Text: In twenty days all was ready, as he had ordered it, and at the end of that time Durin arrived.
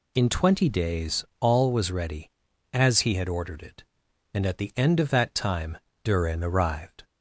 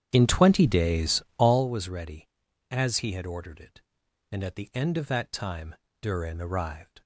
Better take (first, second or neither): first